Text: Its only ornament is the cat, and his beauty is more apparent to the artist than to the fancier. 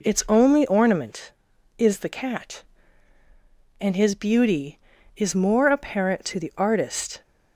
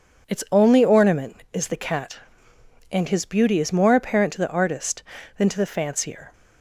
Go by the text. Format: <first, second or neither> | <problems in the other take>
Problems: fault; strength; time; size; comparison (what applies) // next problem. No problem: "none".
second | stops before "than to the fancier"; at 7.2 s